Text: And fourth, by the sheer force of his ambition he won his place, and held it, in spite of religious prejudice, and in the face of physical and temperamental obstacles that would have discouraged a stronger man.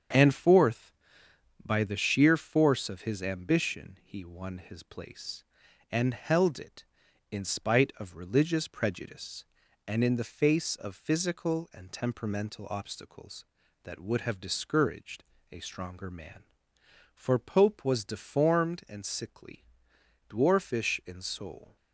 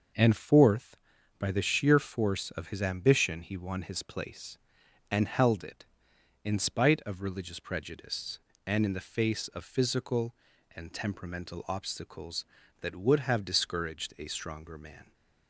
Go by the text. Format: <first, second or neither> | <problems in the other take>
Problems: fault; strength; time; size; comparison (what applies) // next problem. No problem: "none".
second | starts louder than the rest; strong; until 1.8 s; 7.5 dB // pauses between "discouraged" and "a"; slight; at 15.2 s; 0.26 s long // goes on to say "For Pope was deformed and sickly dwarfish in soul"; strong; from 17.1 s on; 4.6 s long